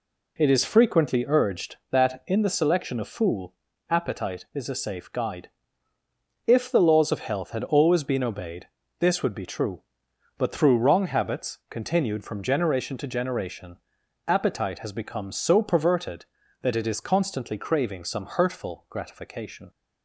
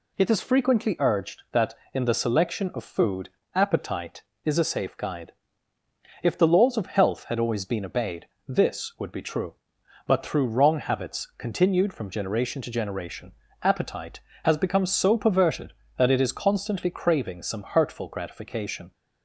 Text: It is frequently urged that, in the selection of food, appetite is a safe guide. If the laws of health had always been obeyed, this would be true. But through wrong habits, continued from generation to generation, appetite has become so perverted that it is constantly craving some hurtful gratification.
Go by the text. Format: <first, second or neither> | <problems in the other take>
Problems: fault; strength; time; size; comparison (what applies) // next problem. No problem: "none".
second | says "fool" for "food"; at 3.0 s